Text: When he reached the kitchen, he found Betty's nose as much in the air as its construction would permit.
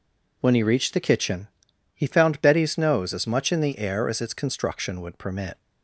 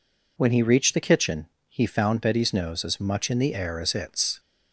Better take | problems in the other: first | stops before "construction would permit"; at 4.3 s

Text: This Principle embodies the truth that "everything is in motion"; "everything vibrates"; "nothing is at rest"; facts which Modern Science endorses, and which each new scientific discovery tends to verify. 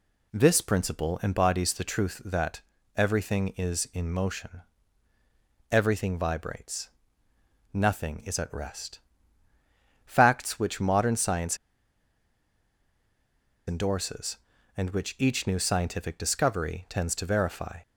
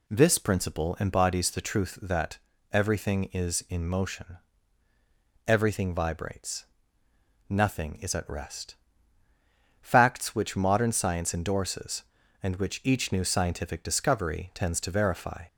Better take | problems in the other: second | pauses between "that" and "everything"; slight; at 2.5 s; 0.36 s long; slight in the second // pauses between "Science" and "endorses"; strong; at 11.5 s; 2.1 s long

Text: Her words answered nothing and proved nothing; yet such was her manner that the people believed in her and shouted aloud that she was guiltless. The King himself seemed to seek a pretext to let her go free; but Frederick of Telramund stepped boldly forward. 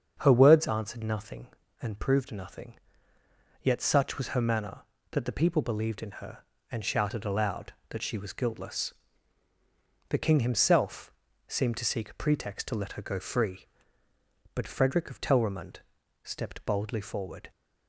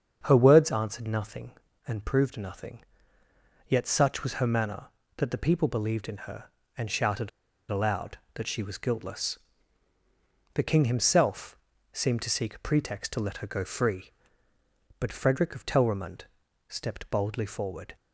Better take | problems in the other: first | starts louder than the rest; strong; until 1.2 s; 7 dB; strong in the first // pauses between "shouted" and "aloud"; at 7.2 s; 0.41 s long // pauses between "himself" and "seemed"; slight; at 11.5 s; 0.36 s long; slight in the first // pauses between "Telramund" and "stepped"; at 16.2 s; 0.44 s long; also in the first

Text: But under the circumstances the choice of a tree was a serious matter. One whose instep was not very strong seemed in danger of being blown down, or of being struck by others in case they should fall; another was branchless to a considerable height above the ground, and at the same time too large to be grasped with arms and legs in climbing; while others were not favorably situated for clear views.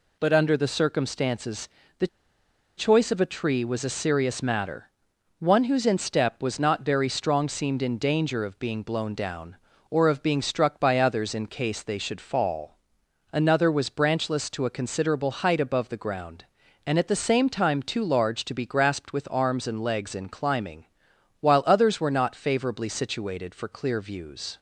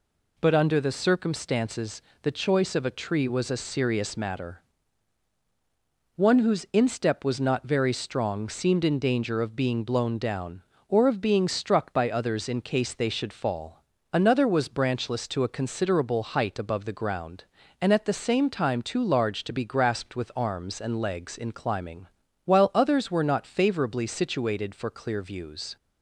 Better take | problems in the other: second | pauses between "circumstances" and "the"; slight; at 1.6 s; 0.30 s long; slight in the second // pauses between "the" and "choice"; noticeable; at 2.0 s; 0.71 s long

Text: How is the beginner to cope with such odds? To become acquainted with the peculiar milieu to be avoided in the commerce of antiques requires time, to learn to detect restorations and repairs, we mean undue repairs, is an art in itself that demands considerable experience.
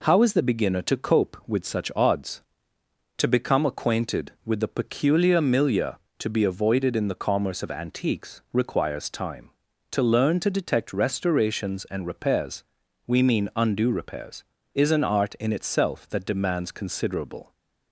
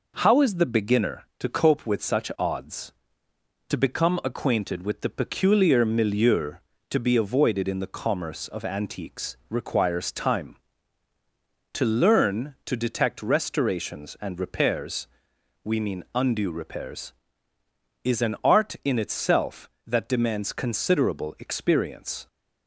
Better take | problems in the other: second | stops before "experience"; at 17.5 s

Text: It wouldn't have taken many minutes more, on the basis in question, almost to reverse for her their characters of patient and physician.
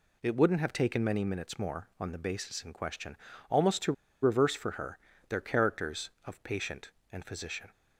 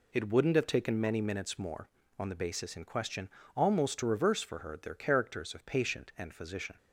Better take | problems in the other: second | pauses between "to" and "reverse"; slight; at 3.9 s; 0.30 s long // pauses between "her" and "their"; slight; at 4.9 s; 0.30 s long

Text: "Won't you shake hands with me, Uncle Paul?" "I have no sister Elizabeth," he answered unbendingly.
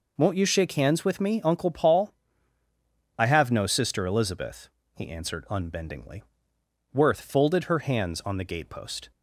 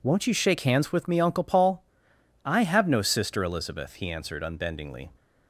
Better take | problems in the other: second | goes on to say "Worth folded her hands on the gatepost"; strong; from 6.9 s on; 2.2 s long

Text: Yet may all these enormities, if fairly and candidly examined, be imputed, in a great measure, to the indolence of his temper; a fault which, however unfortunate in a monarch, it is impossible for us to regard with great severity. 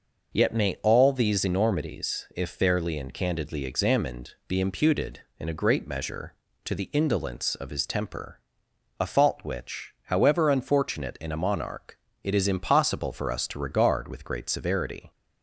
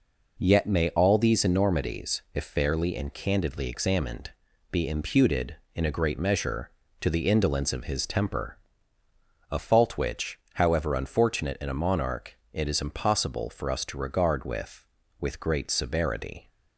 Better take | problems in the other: first | says "with" twice; at 15.1 s

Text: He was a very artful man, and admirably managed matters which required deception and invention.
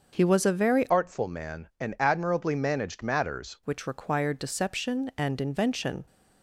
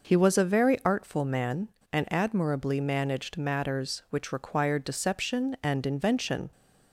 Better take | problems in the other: second | starts louder than the rest; until 1.1 s; 6.5 dB // changes voice from "artful" to "matters"; from 0.8 to 3.5 s; 2.7 s long

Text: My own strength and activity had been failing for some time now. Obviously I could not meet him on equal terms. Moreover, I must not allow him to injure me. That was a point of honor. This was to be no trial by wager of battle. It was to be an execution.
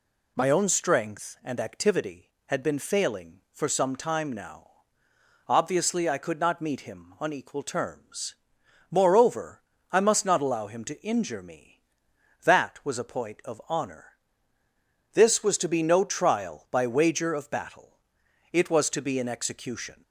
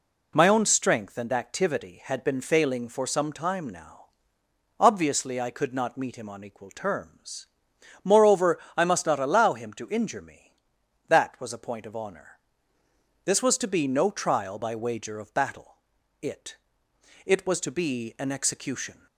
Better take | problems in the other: first | says "It" twice; at 17.2 s

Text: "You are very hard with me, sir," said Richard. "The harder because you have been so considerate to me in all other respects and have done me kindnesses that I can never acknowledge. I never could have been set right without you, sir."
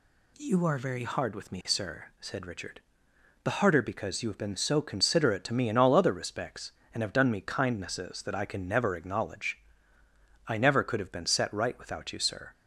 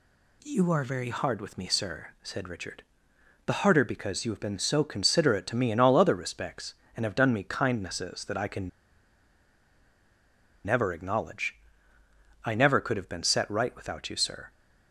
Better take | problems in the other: first | pauses between "can" and "never"; strong; at 8.6 s; 1.9 s long

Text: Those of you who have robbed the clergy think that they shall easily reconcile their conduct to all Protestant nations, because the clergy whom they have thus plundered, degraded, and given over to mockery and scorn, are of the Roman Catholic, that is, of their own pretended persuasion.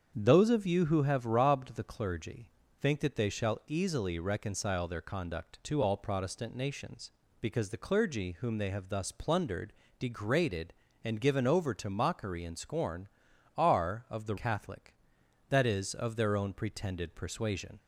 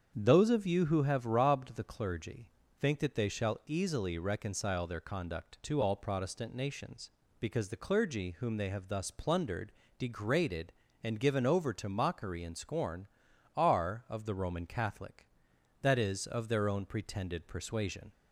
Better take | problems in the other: second | starts louder than the rest; strong; until 1.1 s; 7.5 dB; strong in the second // pauses between "clergy" and "think"; slight; at 2.4 s; 0.34 s long; slight in the second // skips "Roman"; at 14.3 s

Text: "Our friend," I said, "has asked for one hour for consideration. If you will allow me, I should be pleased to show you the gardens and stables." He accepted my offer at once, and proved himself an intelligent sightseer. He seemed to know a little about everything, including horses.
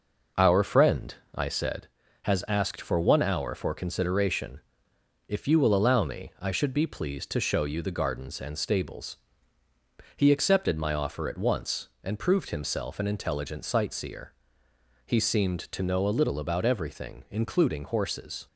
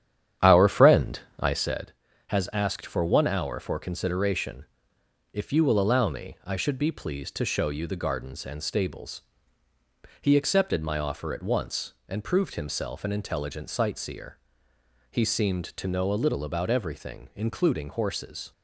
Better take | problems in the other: first | starts louder than the rest; strong; until 1.7 s; 9.5 dB

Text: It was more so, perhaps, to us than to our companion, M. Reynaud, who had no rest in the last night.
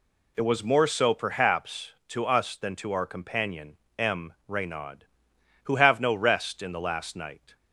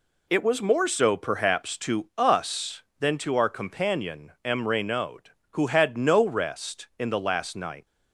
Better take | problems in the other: second | says "have" for "had"; at 5.7 s

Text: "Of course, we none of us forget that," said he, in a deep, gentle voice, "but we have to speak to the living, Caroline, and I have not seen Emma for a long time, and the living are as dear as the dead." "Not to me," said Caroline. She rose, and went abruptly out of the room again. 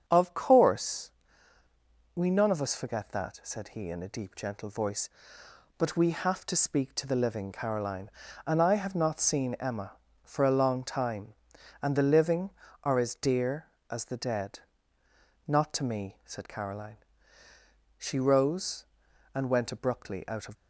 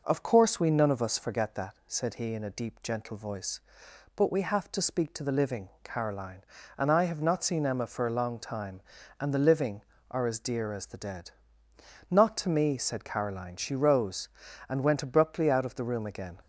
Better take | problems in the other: second | starts louder than the rest; strong; until 1.0 s; 8 dB // stops before "the room again"; at 20.5 s

